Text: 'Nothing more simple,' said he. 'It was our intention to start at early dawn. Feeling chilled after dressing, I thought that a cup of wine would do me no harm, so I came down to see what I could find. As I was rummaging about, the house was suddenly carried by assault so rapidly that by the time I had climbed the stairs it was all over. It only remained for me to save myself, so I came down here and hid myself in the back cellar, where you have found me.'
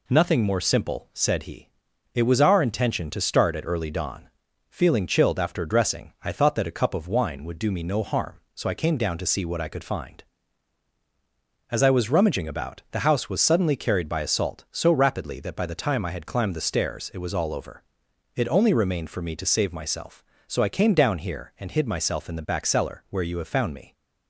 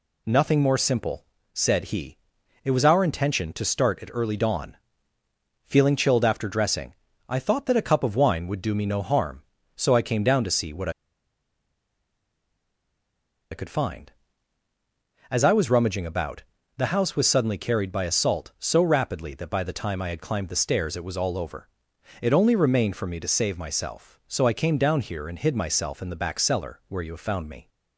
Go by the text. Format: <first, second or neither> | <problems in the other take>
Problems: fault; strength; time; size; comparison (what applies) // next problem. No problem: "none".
first | pauses between "what" and "I"; strong; at 10.8 s; 2.6 s long